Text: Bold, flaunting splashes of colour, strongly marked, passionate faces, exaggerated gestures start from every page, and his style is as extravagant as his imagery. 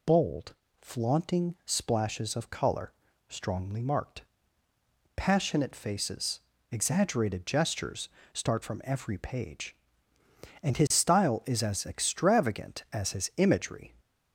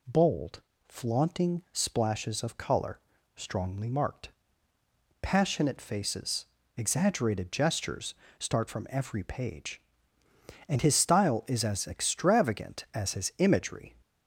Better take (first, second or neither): second